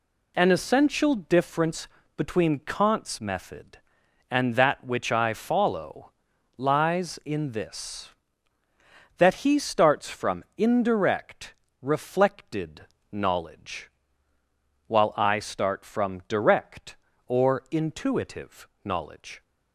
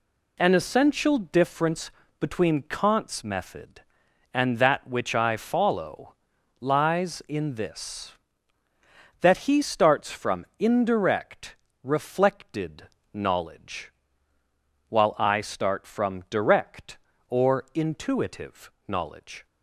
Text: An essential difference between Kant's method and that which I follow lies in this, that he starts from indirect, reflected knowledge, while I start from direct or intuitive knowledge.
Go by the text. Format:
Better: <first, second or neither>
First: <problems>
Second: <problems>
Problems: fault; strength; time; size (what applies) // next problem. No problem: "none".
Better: neither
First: pauses between "difference" and "between"; slight; at 1.8 s; 0.30 s long // pauses between "follow" and "lies"; noticeable; at 6.1 s; 0.46 s long // pauses between "reflected" and "knowledge"; slight; at 12.8 s; 0.30 s long // pauses between "intuitive" and "knowledge"; slight; at 18.6 s; 0.16 s long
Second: pauses between "difference" and "between"; slight; at 1.8 s; 0.30 s long // pauses between "follow" and "lies"; noticeable; at 6.1 s; 0.46 s long // pauses between "reflected" and "knowledge"; slight; at 12.8 s; 0.30 s long // pauses between "intuitive" and "knowledge"; slight; at 18.7 s; 0.16 s long